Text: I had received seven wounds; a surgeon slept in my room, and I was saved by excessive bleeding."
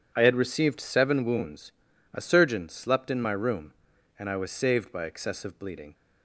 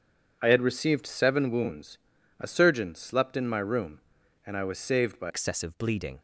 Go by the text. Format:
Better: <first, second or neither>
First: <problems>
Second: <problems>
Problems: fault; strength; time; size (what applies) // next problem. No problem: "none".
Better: first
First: none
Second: changes voice at "excessive"; from 5.2 s on; 0.9 s long